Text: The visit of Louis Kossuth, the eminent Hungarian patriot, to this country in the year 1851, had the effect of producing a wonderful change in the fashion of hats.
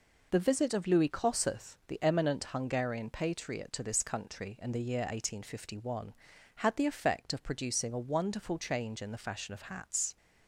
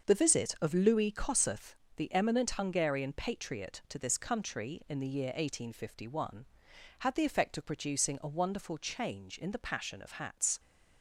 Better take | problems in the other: first | starts louder than the rest; until 1.1 s; 6.5 dB // says "passion" for "fashion"; at 9.6 s

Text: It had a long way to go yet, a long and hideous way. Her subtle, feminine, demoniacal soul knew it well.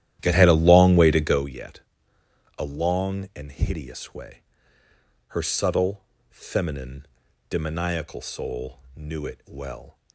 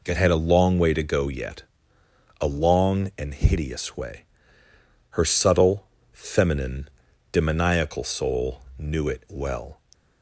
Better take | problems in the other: second | starts louder than the rest; strong; until 1.5 s; 12.5 dB // pauses between "soul" and "knew"; slight; at 8.8 s; 0.16 s long; slight in the second

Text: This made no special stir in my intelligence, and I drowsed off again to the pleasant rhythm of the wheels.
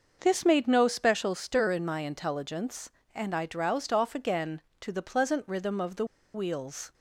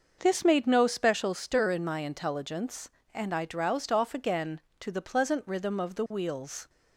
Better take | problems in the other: second | starts louder than the rest; noticeable; until 1.2 s; 6 dB; noticeable in the second // pauses between "the" and "wheels"; slight; at 6.0 s; 0.30 s long

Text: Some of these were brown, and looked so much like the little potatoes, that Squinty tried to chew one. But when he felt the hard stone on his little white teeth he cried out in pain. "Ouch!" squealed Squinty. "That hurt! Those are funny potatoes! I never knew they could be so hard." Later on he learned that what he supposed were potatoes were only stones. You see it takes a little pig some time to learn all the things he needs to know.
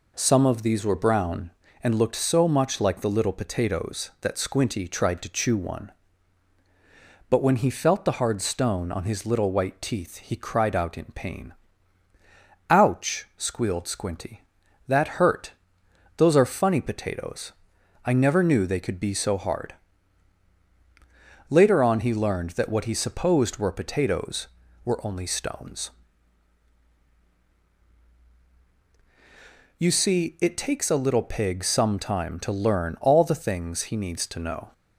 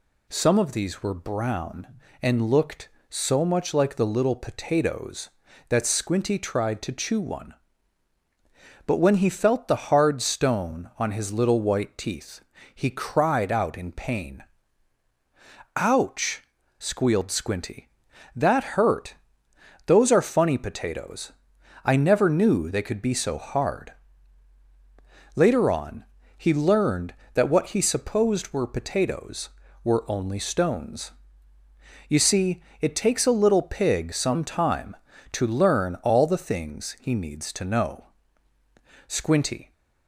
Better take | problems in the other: first | pauses between "teeth" and "he"; slight; at 12.4 s; 0.34 s long // pauses between "on" and "he"; slight; at 26.0 s; 0.32 s long // pauses between "see" and "it"; slight; at 32.6 s; 0.18 s long // goes on to say "Squinty"; noticeable; from 39.0 s on; 0.64 s long

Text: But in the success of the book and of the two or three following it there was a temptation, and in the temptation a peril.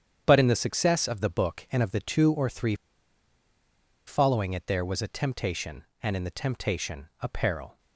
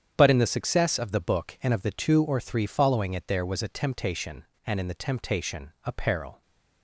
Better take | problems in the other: second | starts louder than the rest; strong; until 1.2 s; 8.5 dB; strong in the second // pauses between "three" and "following"; strong; at 2.7 s; 1.3 s long

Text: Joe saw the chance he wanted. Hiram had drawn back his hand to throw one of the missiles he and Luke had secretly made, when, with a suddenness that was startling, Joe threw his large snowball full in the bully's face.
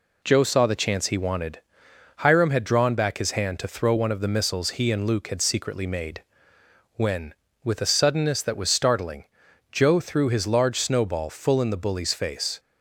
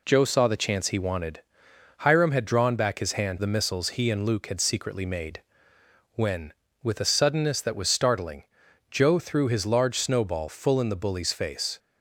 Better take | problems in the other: first | skips "to throw one of"; at 3.3 s

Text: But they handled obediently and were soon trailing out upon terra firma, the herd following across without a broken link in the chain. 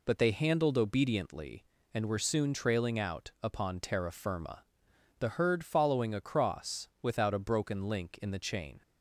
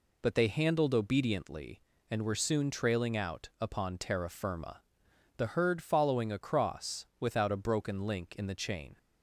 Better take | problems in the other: neither | none

